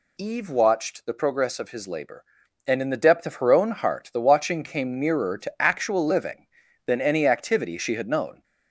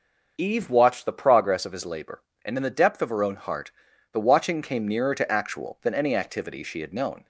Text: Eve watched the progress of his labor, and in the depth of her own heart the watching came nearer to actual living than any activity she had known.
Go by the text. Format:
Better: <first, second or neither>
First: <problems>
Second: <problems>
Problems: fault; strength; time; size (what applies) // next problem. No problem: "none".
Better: first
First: none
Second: starts louder than the rest; until 1.3 s; 6 dB // pauses between "heart" and "the"; at 3.7 s; 0.42 s long // skips "living"; at 5.7 s